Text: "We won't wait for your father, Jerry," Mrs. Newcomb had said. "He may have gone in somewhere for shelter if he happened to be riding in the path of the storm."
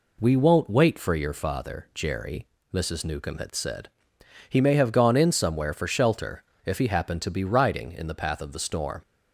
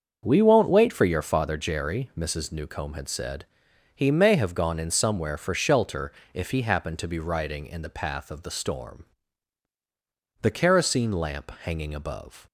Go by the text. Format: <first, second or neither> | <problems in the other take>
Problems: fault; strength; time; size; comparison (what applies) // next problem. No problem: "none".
first | starts louder than the rest; until 1.2 s; 7 dB // pauses between "shelter" and "if"; slight; at 6.1 s; 0.20 s long; slight in the first // goes on to say "The kerosene lamp hanging above"; strong; from 10.4 s on; 2.0 s long